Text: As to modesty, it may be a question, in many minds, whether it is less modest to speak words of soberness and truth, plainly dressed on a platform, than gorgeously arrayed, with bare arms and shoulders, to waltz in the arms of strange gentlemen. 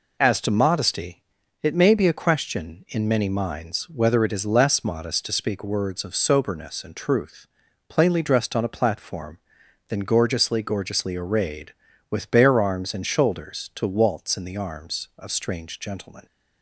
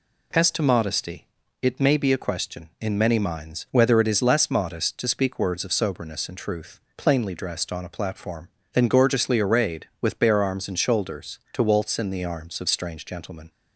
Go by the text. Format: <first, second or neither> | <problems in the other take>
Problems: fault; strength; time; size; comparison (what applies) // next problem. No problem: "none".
second | says "gorgeously" twice; at 10.6 s